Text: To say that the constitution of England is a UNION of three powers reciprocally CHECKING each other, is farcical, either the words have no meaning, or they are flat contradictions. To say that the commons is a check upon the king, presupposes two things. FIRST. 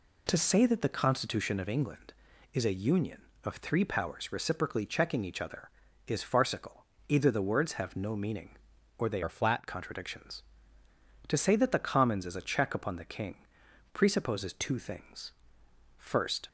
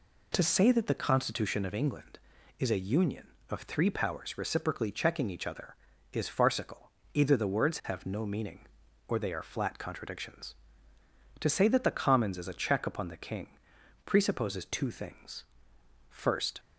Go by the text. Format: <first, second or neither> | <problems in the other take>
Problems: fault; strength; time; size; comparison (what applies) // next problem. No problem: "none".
second | changes voice from "are" to "flat"; from 9.2 to 9.6 s; 0.4 s long